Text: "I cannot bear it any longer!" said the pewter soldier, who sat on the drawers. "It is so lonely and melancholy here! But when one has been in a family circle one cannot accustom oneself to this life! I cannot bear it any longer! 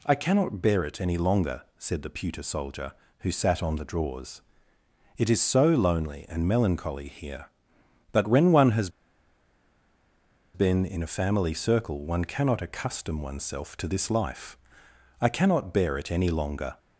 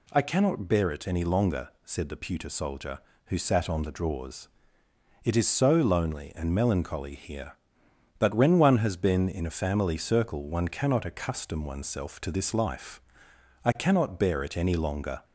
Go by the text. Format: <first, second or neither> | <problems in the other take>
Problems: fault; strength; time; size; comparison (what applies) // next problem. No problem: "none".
second | pauses between "has" and "been"; strong; at 8.8 s; 1.6 s long